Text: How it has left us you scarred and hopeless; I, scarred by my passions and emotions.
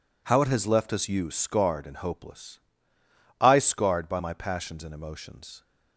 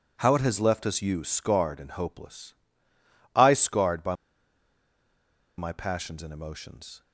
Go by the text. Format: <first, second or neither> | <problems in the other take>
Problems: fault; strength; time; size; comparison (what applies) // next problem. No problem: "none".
first | pauses between "by" and "my"; strong; at 4.1 s; 1.4 s long